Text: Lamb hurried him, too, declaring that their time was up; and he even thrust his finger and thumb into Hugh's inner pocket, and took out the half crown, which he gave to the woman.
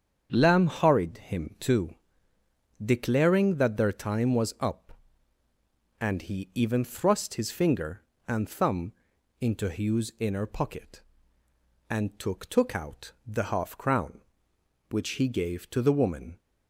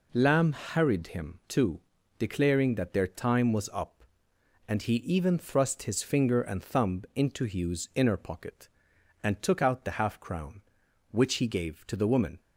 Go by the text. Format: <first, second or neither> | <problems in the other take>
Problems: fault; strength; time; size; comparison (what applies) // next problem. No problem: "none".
second | starts louder than the rest; strong; until 1.3 s; 7.5 dB // pauses between "thumb" and "into"; noticeable; at 8.9 s; 0.48 s long // says "took" twice; at 12.4 s // pauses between "out" and "the"; slight; at 13.1 s; 0.16 s long